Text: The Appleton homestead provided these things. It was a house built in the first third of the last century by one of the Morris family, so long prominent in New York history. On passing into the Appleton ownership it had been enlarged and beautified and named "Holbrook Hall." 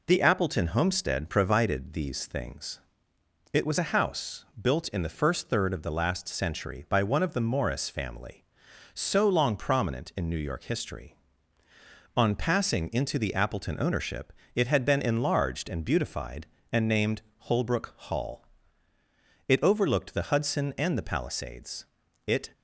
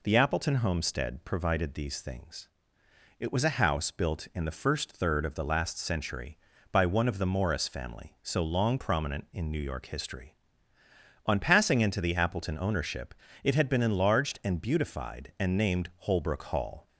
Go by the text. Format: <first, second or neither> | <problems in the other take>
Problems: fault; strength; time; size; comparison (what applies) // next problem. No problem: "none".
second | pauses between "house" and "built"; slight; at 4.4 s; 0.16 s long // pauses between "ownership" and "it"; slight; at 14.3 s; 0.24 s long; slight in the second // pauses between "named" and "Holbrook"; slight; at 17.2 s; 0.16 s long // goes on to say "It overlooked the Hudson and the Palisades It"; strong; from 19.4 s on; 3.0 s long